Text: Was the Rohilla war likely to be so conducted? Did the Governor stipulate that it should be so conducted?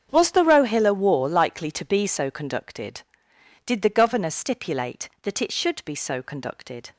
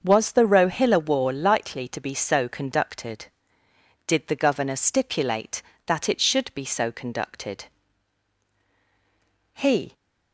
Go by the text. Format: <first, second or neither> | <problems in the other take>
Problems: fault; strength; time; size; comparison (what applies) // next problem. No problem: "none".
first | starts louder than the rest; until 1.0 s; 6.5 dB; strong in the first // goes on to say "He"; slight; from 9.5 s on; 0.40 s long